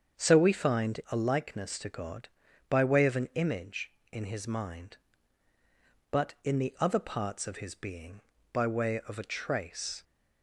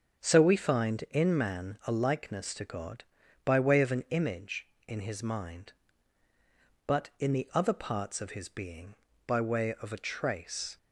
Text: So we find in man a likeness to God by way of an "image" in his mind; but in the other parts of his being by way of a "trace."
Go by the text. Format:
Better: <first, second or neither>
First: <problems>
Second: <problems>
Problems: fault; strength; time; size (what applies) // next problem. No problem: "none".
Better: second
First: starts louder than the rest; strong; until 1.3 s; 7 dB // skips "in man"; at 1.0 s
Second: starts louder than the rest; until 1.2 s; 7 dB